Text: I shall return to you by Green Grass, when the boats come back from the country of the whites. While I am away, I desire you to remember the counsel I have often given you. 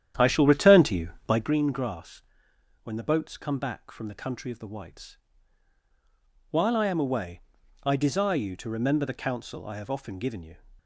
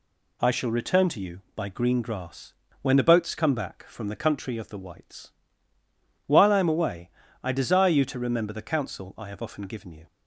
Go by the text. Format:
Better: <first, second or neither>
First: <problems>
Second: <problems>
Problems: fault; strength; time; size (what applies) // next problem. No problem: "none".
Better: second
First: starts louder than the rest; strong; until 1.6 s; 10 dB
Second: none